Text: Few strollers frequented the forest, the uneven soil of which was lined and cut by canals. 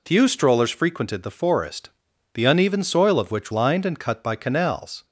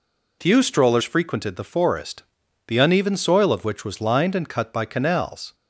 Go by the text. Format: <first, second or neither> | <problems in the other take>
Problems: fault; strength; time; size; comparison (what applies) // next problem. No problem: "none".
second | skips "was"; at 3.5 s